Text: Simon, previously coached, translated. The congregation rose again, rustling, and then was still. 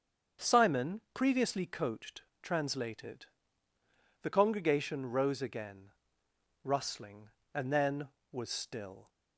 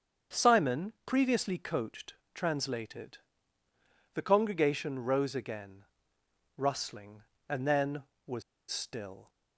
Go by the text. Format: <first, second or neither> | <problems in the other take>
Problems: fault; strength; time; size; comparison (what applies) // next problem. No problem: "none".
first | starts louder than the rest; until 1.4 s; 6.5 dB; also in the first // pauses between "was" and "still"; slight; at 8.4 s; 0.28 s long